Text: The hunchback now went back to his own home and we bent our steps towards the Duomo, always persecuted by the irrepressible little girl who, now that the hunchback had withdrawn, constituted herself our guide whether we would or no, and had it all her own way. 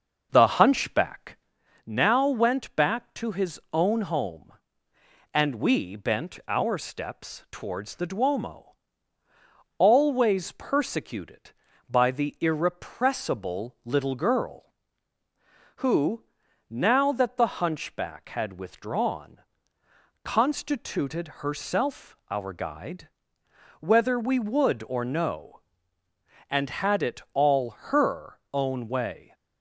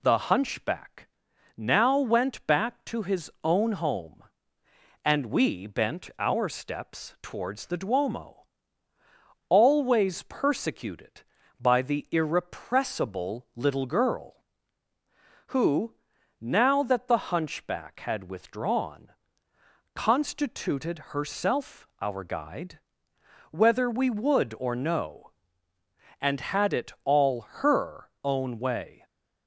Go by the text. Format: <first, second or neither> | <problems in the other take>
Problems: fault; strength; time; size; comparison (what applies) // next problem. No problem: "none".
second | starts louder than the rest; noticeable; until 1.7 s; 6 dB // pauses between "hunchback" and "now"; noticeable; at 1.3 s; 0.48 s long; noticeable in the second // pauses between "guide" and "whether"; noticeable; at 23.0 s; 0.72 s long; noticeable in the second